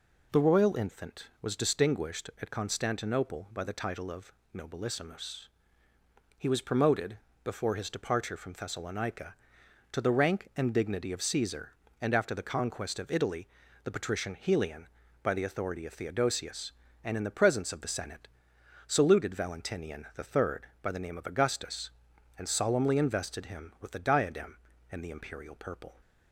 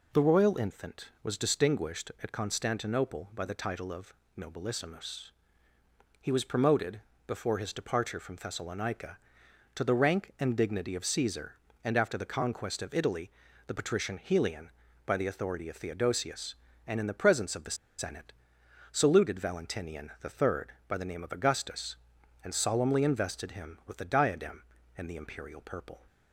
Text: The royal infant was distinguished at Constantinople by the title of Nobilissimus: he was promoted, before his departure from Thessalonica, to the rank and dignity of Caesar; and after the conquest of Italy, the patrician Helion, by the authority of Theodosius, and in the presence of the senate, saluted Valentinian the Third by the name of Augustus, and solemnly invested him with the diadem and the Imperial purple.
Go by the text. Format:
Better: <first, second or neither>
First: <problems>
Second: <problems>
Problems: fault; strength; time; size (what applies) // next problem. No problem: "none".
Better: first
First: pauses between "of" and "Nobilissimus"; slight; at 4.3 s; 0.22 s long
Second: pauses between "of" and "Nobilissimus"; slight; at 4.1 s; 0.24 s long // pauses between "the" and "senate"; slight; at 17.7 s; 0.22 s long